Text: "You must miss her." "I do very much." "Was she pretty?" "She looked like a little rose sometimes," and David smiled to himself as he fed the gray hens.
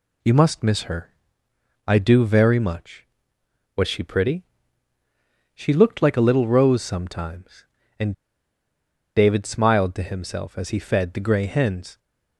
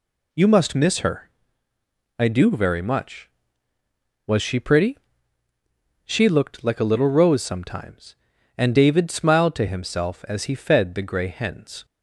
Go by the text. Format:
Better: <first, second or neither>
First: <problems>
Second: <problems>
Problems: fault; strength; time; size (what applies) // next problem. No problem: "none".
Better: second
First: pauses between "and" and "David"; at 8.1 s; 1.0 s long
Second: none